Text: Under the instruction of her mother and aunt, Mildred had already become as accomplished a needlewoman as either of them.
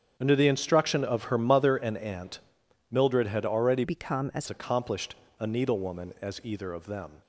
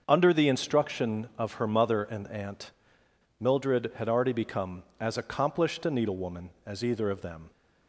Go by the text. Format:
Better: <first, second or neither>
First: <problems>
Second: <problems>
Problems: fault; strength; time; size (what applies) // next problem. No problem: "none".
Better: second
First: starts louder than the rest; strong; until 1.1 s; 7.5 dB // changes voice from "become" to "as"; from 3.8 to 4.4 s; 0.6 s long // pauses between "accomplished" and "a"; slight; at 5.1 s; 0.24 s long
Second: starts louder than the rest; until 1.0 s; 6.5 dB